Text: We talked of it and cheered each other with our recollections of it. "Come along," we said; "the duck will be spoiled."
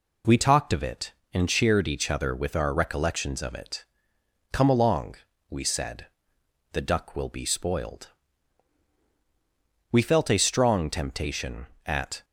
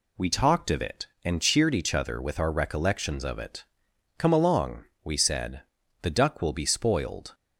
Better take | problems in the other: second | goes on to say "We felt a strong temptation at"; strong; from 9.9 s on; 2.3 s long

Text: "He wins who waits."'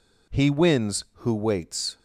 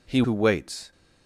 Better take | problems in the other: first | skips "wins"; at 0.2 s

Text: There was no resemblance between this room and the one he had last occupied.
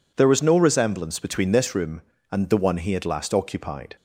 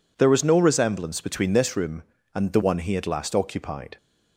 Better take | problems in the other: neither | none

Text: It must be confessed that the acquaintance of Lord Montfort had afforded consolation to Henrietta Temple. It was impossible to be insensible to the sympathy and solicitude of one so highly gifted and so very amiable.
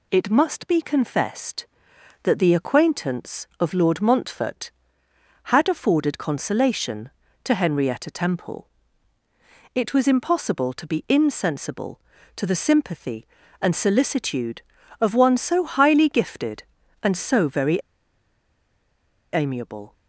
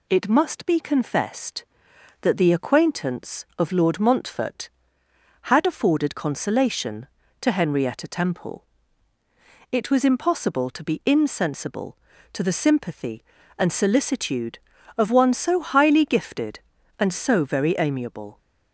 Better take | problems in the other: second | pauses between "very" and "amiable"; strong; at 17.7 s; 1.5 s long

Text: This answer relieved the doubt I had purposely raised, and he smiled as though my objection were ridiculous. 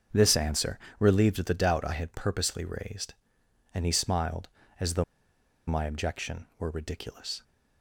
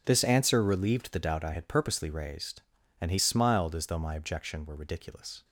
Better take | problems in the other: second | starts louder than the rest; strong; until 1.3 s; 7 dB // pauses between "answer" and "relieved"; slight; at 0.7 s; 0.22 s long // pauses between "though" and "my"; noticeable; at 5.0 s; 0.64 s long

